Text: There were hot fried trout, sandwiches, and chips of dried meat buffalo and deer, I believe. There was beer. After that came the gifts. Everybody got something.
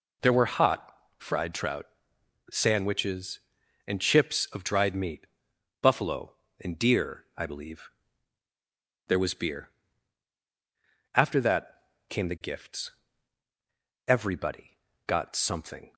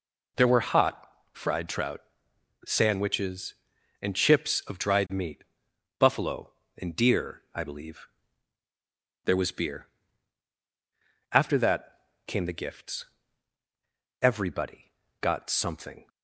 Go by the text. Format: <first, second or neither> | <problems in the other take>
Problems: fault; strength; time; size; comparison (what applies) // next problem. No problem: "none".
neither | pauses between "hot" and "fried"; slight; the same in both // pauses between "meat" and "buffalo"; noticeable; the same in both // pauses between "that" and "came"; slight; the same in both // pauses between "Everybody" and "got"; slight; the same in both